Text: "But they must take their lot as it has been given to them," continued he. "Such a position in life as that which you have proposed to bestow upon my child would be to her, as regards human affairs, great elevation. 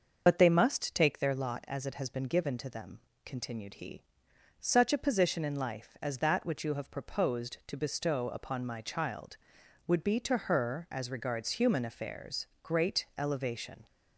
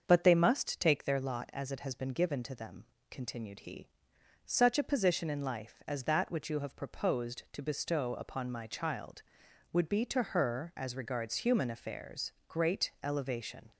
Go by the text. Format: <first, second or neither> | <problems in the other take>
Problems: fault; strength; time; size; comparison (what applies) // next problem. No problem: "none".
second | loses the start of "But"; at 0.2 s; 50 ms // starts louder than the rest; until 1.2 s; 6 dB; also in the second